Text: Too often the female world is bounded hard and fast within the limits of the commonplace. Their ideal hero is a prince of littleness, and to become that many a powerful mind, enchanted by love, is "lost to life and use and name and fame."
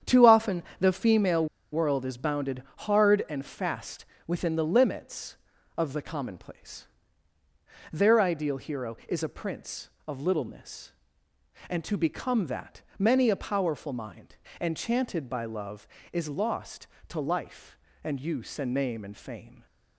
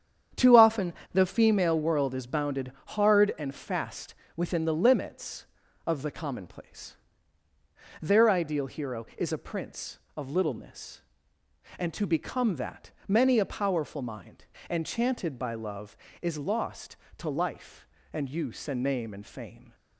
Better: second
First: starts louder than the rest; strong; until 1.2 s; 8.5 dB // pauses between "often" and "the"; slight; at 0.6 s; 0.16 s long // pauses between "female" and "world"; slight; at 1.4 s; 0.27 s long // pauses between "bounded" and "hard"; slight; at 2.6 s; 0.16 s long // pauses between "fast" and "within"; slight; at 4.0 s; 0.22 s long // pauses between "that" and "many"; slight; at 12.8 s; 0.16 s long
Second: starts louder than the rest; strong; until 1.5 s; 8.5 dB // pauses between "often" and "the"; slight; at 0.9 s; 0.19 s long // pauses between "bounded" and "hard"; slight; at 2.7 s; 0.16 s long // pauses between "fast" and "within"; slight; at 4.1 s; 0.22 s long // pauses between "that" and "many"; slight; at 12.9 s; 0.16 s long

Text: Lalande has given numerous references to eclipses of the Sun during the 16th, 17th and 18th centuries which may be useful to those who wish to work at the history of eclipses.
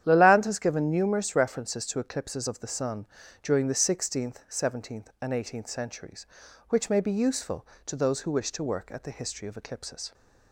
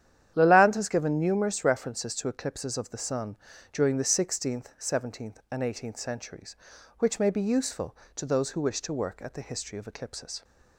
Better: neither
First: starts louder than the rest; strong; until 1.0 s; 10 dB // pauses between "Sun" and "during"; slight; at 3.0 s; 0.34 s long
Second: starts louder than the rest; strong; until 1.3 s; 10 dB // pauses between "Sun" and "during"; slight; at 3.3 s; 0.34 s long

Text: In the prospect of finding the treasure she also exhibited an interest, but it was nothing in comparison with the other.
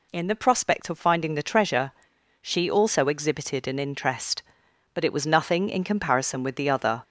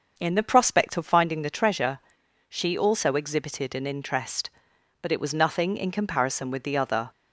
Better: first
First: pauses between "treasure" and "she"; noticeable; at 1.9 s; 0.50 s long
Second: starts louder than the rest; until 1.3 s; 6 dB // pauses between "treasure" and "she"; noticeable; at 1.9 s; 0.50 s long

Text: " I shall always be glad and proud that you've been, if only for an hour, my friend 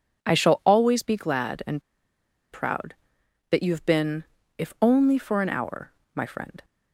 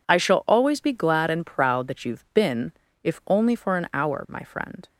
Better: second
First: pauses between "and" and "proud"; noticeable; at 1.8 s; 0.71 s long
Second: none

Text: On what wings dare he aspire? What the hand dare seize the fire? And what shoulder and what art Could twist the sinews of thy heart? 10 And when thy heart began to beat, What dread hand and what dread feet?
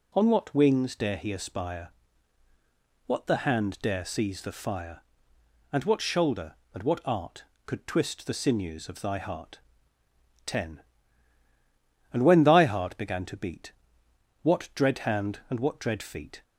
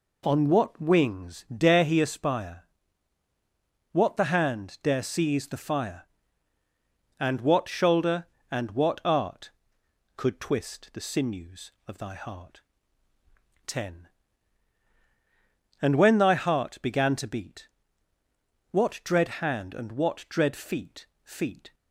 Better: first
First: none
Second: says "feet" twice; at 21.2 s

